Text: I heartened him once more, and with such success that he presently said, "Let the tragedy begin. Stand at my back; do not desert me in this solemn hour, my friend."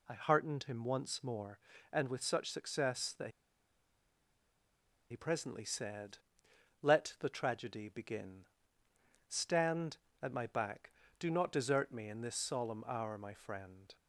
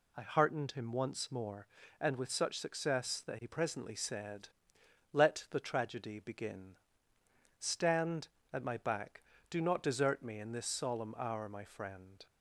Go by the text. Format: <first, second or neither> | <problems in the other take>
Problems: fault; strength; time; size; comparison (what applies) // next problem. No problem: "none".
second | pauses between "that" and "he"; strong; at 3.3 s; 1.8 s long